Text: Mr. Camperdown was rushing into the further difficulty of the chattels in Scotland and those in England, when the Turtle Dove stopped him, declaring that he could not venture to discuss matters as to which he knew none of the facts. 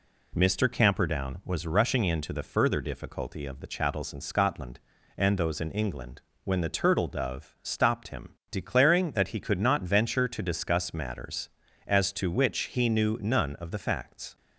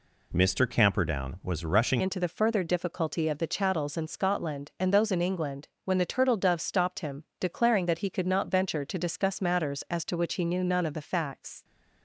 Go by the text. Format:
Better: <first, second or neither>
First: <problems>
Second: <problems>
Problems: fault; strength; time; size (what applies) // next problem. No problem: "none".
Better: first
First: none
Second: changes voice at "into"; from 1.9 s on; 9.7 s long